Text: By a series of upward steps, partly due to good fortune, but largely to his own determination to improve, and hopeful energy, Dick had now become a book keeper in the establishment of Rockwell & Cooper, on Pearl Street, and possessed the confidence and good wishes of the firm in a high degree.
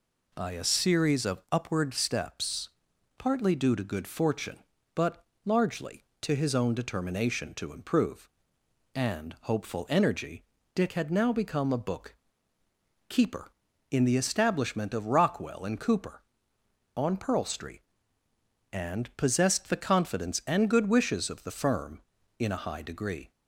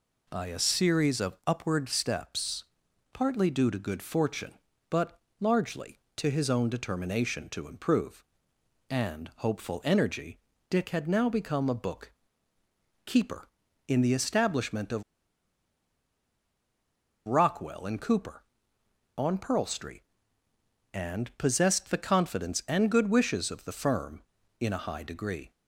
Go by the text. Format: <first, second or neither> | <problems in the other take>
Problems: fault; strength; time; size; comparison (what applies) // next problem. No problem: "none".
first | pauses between "but" and "largely"; slight; at 5.2 s; 0.18 s long; slight in the first // pauses between "book" and "keeper"; noticeable; at 12.1 s; 0.94 s long; noticeable in the first // pauses between "of" and "Rockwell"; strong; at 15.0 s; 2.2 s long